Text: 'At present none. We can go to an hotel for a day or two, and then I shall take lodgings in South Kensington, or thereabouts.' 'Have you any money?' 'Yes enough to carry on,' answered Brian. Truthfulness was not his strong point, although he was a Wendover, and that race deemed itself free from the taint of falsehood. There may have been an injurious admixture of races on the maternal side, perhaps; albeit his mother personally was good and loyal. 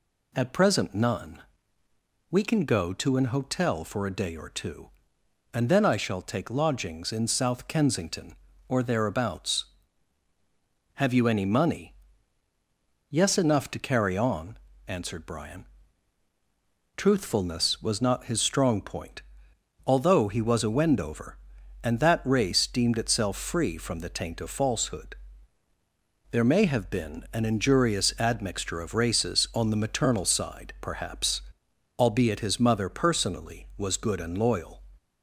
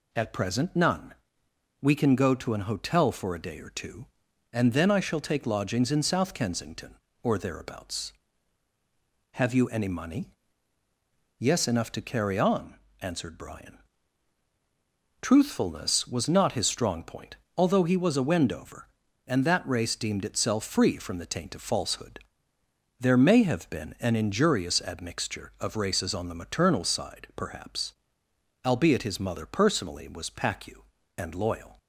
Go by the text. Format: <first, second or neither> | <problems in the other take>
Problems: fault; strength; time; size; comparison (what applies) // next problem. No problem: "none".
first | says "pacu" for "good"; at 30.2 s